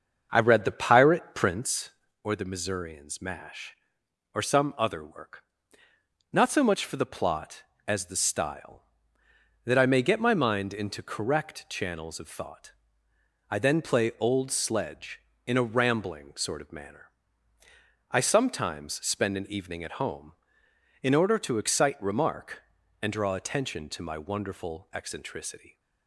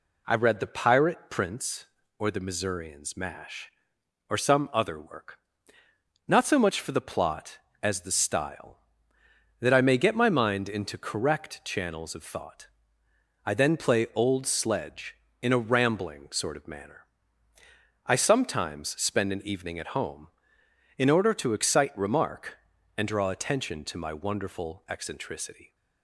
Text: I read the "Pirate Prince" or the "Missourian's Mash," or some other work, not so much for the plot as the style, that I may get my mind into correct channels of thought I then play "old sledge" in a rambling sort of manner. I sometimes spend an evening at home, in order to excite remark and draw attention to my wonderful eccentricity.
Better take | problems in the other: second | starts louder than the rest; until 2.2 s; 7 dB // pauses between "thought" and "I"; noticeable; at 12.7 s; 0.76 s long; noticeable in the second

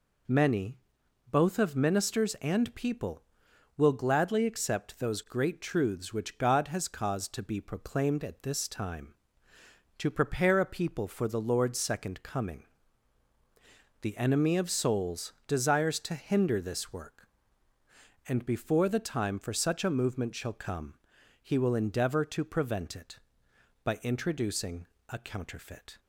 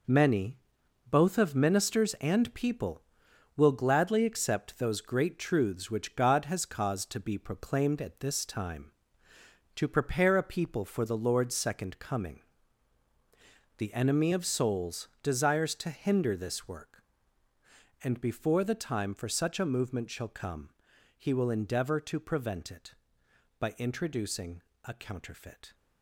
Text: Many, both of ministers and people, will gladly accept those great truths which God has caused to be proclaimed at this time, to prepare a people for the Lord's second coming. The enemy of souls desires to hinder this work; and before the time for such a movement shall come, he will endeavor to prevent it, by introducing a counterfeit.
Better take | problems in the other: first | gets quieter; strong; throughout; 8 dB // pauses between "introducing" and "a"; slight; at 24.6 s; 0.22 s long; slight in the first

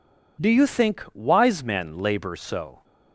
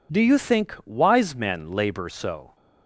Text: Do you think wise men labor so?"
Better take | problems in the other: neither | none

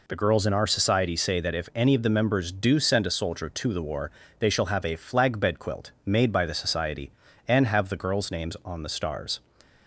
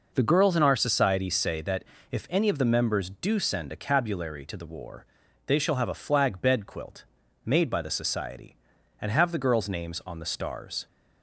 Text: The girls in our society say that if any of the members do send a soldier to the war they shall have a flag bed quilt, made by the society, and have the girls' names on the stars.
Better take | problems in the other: first | pauses between "that" and "if"; slight; at 1.8 s; 0.26 s long // says "cabulary" for "soldier"; at 3.7 s // pauses between "war" and "they"; at 5.0 s; 0.40 s long; slight in the first

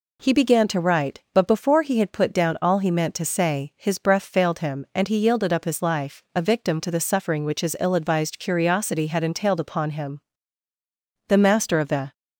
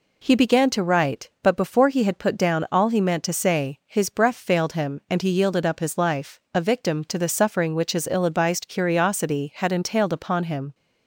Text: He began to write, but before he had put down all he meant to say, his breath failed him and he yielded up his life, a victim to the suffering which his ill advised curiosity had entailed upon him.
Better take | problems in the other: second | goes on to say "The master of the"; noticeable; from 11.2 s on; 0.84 s long

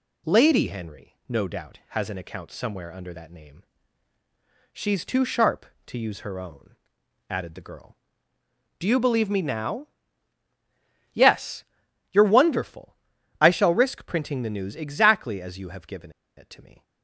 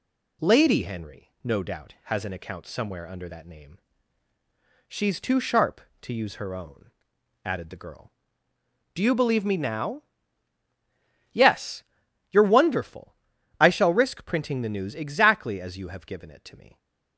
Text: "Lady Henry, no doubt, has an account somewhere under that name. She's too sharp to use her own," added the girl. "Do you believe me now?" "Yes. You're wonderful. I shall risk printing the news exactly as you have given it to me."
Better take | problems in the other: second | pauses between "given" and "it"; slight; at 16.0 s; 0.27 s long

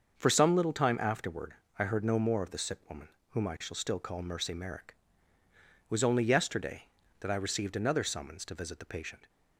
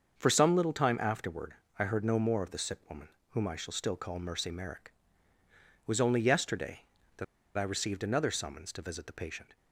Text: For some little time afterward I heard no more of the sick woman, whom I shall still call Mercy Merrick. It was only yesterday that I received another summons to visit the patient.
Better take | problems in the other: first | starts louder than the rest; strong; until 1.2 s; 7 dB; strong in the first // pauses between "afterward" and "I"; slight; at 1.5 s; 0.22 s long; slight in the first // pauses between "that" and "I"; slight; at 7.2 s; 0.32 s long

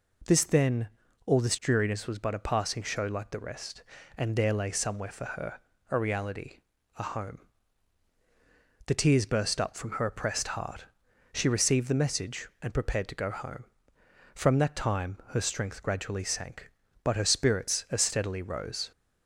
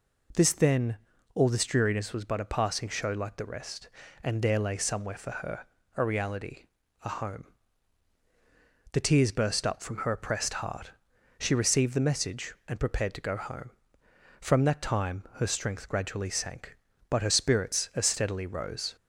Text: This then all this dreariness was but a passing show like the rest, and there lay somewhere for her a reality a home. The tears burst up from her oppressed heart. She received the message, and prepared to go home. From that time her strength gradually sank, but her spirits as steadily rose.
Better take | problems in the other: neither | pauses between "then" and "all"; slight; the same in both // pauses between "her" and "a"; slight; the same in both // pauses between "reality" and "a"; the same in both

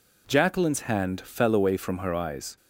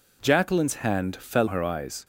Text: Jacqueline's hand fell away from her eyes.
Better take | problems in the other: first | skips "away from"; at 1.4 s

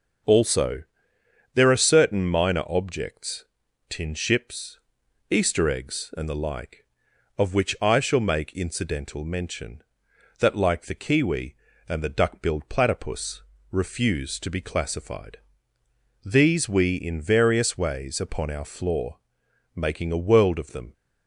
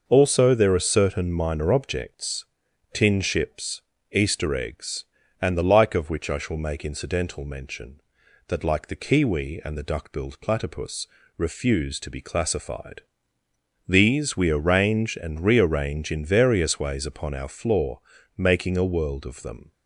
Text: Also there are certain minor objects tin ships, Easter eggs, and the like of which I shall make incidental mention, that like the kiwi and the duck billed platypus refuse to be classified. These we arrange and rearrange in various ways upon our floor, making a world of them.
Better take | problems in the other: second | starts louder than the rest; noticeable; until 1.9 s; 6 dB // pauses between "Also" and "there"; noticeable; at 0.8 s; 0.70 s long // pauses between "objects" and "tin"; at 3.4 s; 0.44 s long; noticeable in the second // pauses between "platypus" and "refuse"; slight; at 13.4 s; 0.28 s long; slight in the second // skips "arrange and rearrange"; at 16.9 s

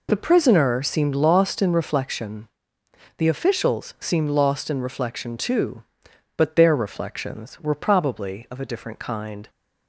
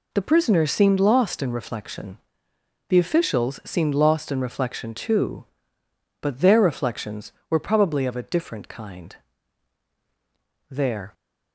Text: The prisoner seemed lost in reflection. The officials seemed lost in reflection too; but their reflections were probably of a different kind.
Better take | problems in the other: first | goes on to say "There"; slight; from 10.6 s on; 0.44 s long

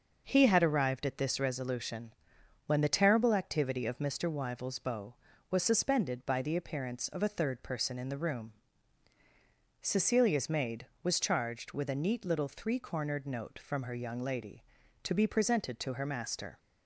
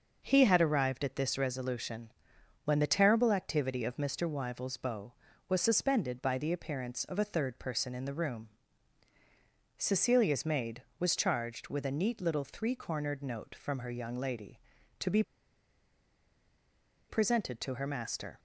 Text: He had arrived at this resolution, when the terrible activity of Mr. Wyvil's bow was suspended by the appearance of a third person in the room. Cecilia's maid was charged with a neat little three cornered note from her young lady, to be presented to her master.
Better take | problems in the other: first | pauses between "be" and "presented"; strong; at 15.2 s; 1.8 s long

